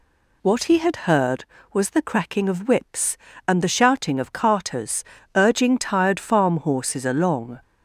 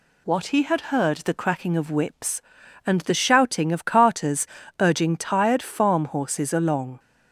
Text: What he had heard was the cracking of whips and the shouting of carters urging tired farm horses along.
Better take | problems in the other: first | skips "was"; at 1.1 s // pauses between "carters" and "urging"; slight; at 4.4 s; 0.34 s long; slight in the first

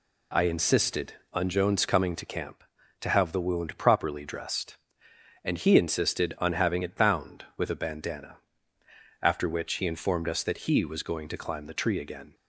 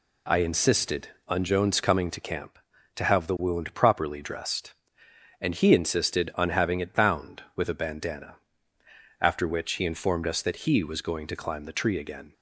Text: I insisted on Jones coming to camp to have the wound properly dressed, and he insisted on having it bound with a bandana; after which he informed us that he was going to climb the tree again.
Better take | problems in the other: neither | none

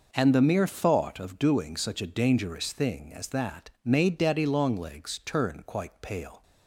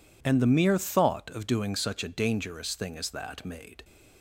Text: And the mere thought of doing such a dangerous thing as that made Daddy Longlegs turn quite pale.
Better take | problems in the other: first | stops before "Daddy Longlegs turn quite pale"; at 3.8 s

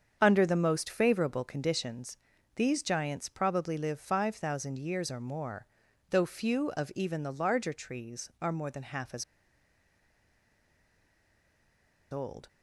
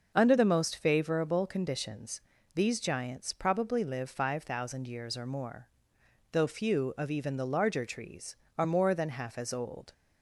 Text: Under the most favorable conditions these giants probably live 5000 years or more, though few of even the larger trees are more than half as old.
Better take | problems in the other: second | starts louder than the rest; strong; until 1.2 s; 7.5 dB; also in the second // pauses between "conditions" and "these"; at 2.1 s; 0.40 s long; slight in the second // pauses between "as" and "old"; strong; at 9.2 s; 2.8 s long

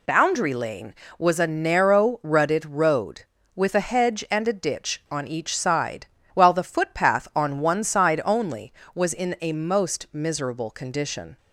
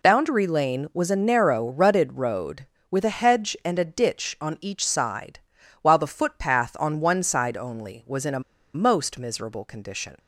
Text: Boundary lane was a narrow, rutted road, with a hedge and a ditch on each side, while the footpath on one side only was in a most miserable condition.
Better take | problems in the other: first | pauses between "a" and "most"; slight; at 8.4 s; 0.34 s long

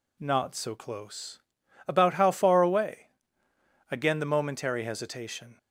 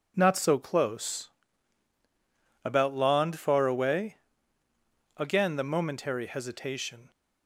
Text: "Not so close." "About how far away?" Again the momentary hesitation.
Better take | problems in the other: first | says "lond" for "how"; at 2.9 s

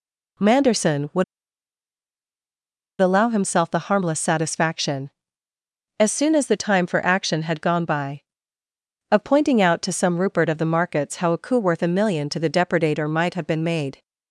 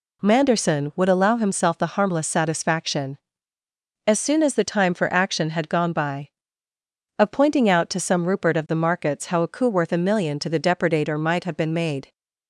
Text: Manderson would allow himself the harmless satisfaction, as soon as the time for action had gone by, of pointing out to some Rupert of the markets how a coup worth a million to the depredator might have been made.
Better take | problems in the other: second | pauses between "would" and "allow"; strong; at 1.2 s; 1.7 s long

